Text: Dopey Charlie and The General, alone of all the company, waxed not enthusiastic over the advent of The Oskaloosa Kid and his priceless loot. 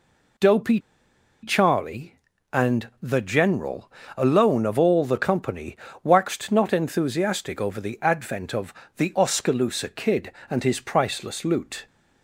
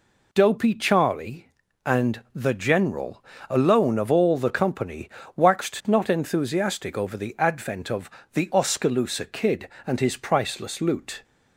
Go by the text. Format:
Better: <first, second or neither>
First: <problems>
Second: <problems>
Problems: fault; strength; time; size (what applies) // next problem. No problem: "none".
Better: second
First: pauses between "Dopey" and "Charlie"; noticeable; at 0.8 s; 0.61 s long // pauses between "of" and "The"; slight; at 8.7 s; 0.24 s long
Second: pauses between "of" and "The"; slight; at 8.0 s; 0.24 s long